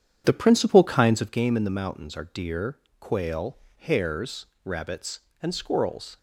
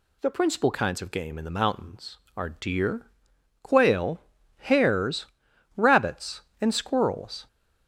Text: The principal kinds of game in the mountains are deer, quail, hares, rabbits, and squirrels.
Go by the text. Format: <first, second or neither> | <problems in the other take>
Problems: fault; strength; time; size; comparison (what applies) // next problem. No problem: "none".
second | starts louder than the rest; strong; until 1.4 s; 9 dB